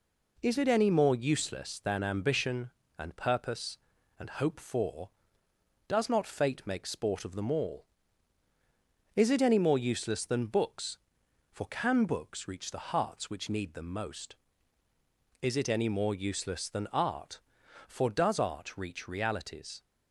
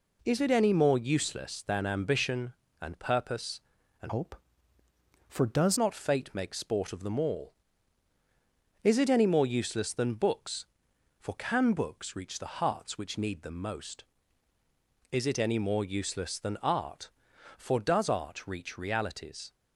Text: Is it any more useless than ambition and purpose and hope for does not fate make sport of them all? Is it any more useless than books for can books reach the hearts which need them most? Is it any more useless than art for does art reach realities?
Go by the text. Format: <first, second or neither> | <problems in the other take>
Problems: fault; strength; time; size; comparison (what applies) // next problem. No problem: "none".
first | changes voice from "hope" to "does"; from 4.0 to 5.7 s; 1.7 s long